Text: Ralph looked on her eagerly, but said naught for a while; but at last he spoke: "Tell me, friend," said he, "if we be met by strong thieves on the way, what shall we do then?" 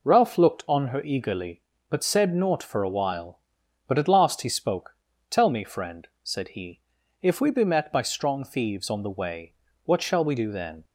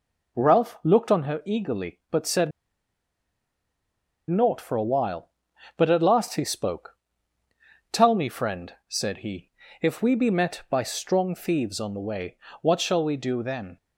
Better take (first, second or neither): first